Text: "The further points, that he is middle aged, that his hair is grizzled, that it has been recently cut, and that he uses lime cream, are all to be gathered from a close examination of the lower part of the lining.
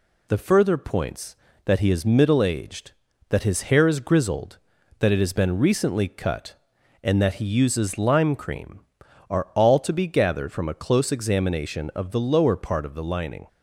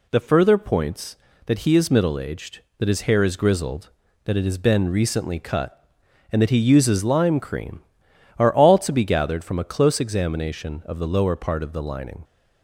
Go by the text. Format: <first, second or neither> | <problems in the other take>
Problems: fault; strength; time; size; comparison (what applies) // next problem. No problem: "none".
neither | none